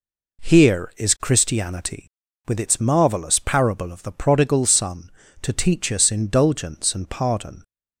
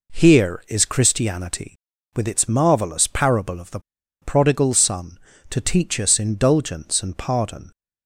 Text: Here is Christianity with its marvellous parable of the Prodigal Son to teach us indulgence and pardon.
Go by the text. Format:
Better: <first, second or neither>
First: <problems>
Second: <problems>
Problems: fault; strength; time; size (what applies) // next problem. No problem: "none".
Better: first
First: none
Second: pauses between "the" and "Prodigal"; at 3.7 s; 0.42 s long